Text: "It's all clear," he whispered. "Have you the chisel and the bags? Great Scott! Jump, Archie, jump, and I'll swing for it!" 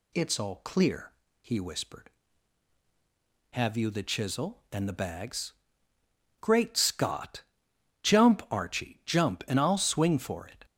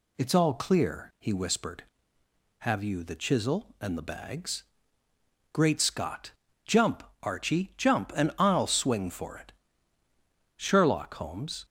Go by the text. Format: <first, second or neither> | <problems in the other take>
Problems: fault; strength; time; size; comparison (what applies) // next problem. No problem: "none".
first | goes on to say "Sherlock Holmes"; noticeable; from 10.5 s on; 1.0 s long